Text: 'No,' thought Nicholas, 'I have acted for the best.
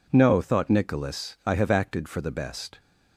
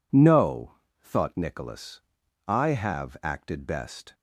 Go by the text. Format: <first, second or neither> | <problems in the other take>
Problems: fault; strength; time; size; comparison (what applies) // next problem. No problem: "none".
first | skips "for the"; at 3.6 s